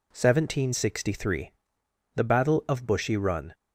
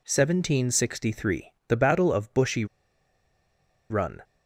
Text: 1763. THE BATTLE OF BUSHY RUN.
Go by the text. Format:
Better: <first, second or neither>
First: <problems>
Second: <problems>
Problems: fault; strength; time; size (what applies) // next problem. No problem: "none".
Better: first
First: none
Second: pauses between "BUSHY" and "RUN"; strong; at 2.6 s; 1.2 s long